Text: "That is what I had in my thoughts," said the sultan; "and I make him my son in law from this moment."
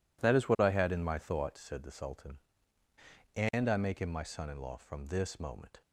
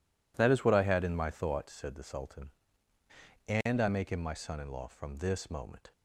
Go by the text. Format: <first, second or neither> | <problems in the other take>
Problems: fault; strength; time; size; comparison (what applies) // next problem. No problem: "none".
neither | none